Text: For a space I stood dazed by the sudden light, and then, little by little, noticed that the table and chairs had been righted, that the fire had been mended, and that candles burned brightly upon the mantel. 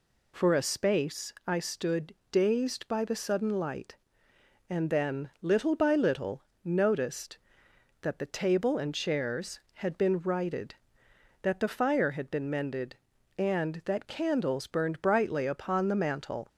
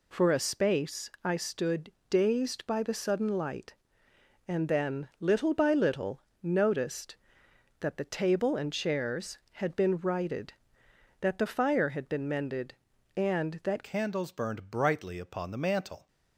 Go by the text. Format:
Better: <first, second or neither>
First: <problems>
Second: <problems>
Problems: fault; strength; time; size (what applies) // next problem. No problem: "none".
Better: first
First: pauses between "stood" and "dazed"; slight; at 2.1 s; 0.18 s long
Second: pauses between "stood" and "dazed"; slight; at 1.8 s; 0.20 s long // changes voice at "candles"; from 13.8 s on; 2.2 s long